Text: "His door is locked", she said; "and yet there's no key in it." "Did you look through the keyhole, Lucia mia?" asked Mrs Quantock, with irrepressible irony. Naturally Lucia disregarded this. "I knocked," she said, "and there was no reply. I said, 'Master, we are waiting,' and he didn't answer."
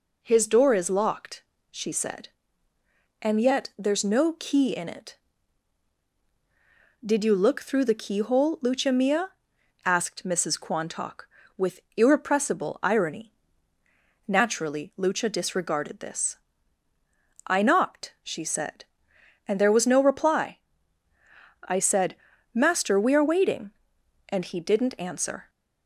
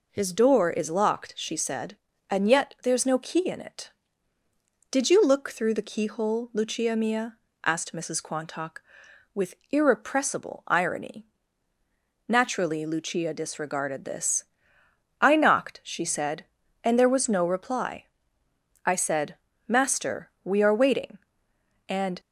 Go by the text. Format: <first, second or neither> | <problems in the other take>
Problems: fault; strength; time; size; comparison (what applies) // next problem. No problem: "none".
first | pauses between "with" and "irrepressible"; slight; at 9.5 s; 0.16 s long; slight in the first // stops before "he didn't answer"; at 22.1 s